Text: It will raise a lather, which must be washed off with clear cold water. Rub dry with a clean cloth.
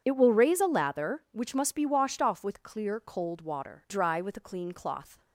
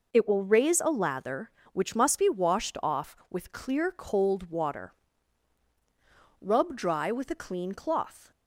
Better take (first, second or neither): second